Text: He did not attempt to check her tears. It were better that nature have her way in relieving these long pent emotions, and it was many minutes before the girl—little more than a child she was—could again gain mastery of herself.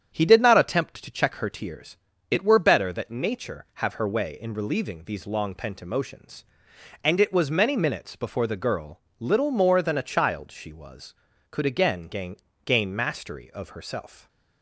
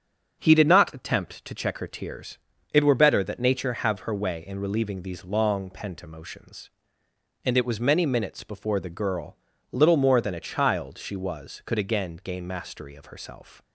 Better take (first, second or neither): second